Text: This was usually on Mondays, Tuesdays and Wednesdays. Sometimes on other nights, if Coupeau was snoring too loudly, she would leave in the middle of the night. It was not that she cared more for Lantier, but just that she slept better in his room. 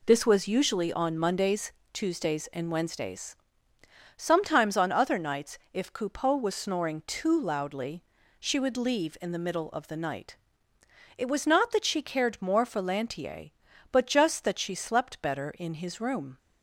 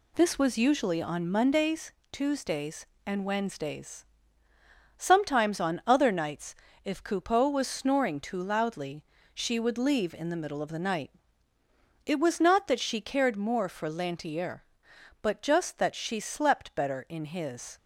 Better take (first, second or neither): first